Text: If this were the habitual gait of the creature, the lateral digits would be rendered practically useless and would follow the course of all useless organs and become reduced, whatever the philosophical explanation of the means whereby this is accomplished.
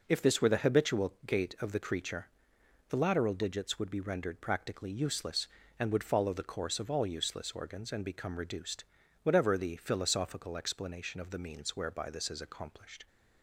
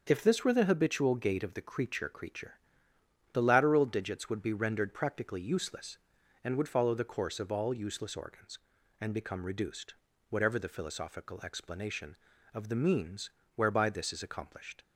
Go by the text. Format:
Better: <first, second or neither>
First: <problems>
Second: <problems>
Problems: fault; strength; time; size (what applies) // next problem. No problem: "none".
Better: first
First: none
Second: starts louder than the rest; until 1.0 s; 7 dB // says "creature" twice; at 2.0 s // pauses between "means" and "whereby"; slight; at 13.2 s; 0.24 s long